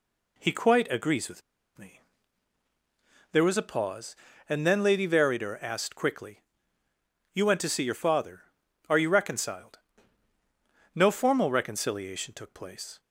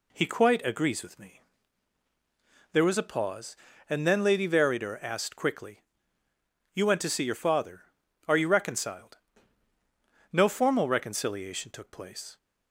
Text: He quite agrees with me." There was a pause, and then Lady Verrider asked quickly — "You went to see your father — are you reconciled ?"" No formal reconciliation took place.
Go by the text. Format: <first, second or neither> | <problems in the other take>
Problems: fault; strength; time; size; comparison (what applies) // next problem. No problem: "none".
second | pauses between "with" and "me"; slight; at 1.4 s; 0.36 s long